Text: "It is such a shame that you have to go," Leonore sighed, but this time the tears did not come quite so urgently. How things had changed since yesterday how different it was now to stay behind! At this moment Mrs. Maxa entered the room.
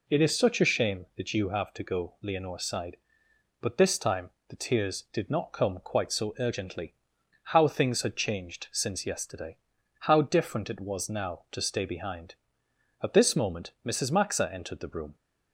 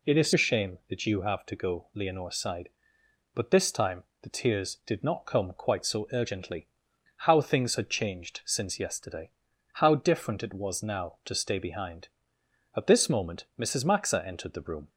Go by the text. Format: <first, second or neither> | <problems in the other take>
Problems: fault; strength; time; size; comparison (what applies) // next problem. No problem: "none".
first | skips "such"; at 0.3 s // pauses between "time" and "the"; slight; at 4.0 s; 0.20 s long; slight in the first // pauses between "yesterday" and "how"; at 9.3 s; 0.44 s long; also in the first